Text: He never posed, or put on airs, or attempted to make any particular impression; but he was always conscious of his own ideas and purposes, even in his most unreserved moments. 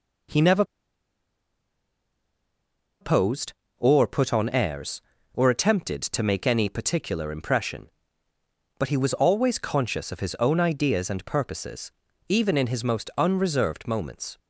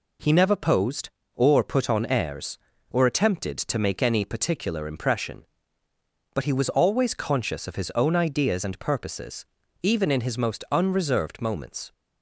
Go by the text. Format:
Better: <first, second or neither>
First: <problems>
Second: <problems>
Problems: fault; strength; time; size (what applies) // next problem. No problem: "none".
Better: second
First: pauses between "never" and "posed"; strong; at 0.6 s; 2.3 s long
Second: none